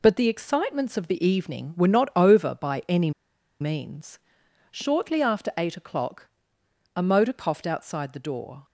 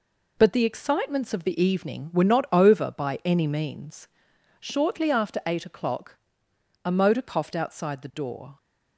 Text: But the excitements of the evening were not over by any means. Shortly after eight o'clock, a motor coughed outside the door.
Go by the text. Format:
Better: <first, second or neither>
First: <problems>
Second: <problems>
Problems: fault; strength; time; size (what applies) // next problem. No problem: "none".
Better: second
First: pauses between "any" and "means"; noticeable; at 3.1 s; 0.49 s long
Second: none